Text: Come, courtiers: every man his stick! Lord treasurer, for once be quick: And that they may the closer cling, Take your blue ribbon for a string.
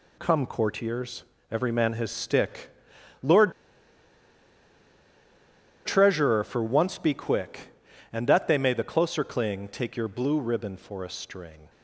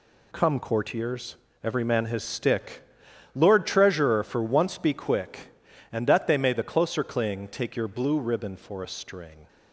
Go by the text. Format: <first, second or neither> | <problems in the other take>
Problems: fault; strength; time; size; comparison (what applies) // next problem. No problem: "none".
second | pauses between "Lord" and "treasurer"; strong; at 3.5 s; 2.3 s long